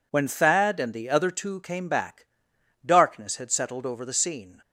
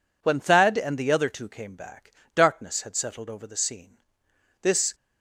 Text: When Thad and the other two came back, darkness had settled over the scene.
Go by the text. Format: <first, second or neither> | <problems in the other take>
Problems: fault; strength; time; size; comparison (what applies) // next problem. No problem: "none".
first | goes on to say "This"; slight; from 4.6 s on; 0.32 s long